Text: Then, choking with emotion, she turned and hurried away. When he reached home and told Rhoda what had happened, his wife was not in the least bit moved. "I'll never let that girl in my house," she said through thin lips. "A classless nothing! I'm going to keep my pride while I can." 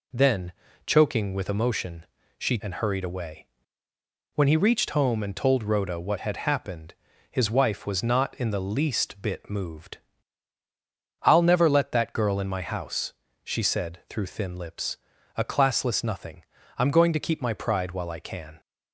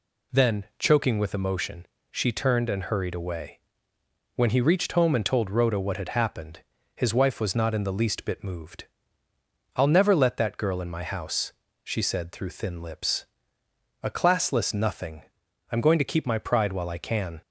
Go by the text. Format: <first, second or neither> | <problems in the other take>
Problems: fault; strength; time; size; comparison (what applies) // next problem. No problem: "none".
second | skips "turned"; at 2.6 s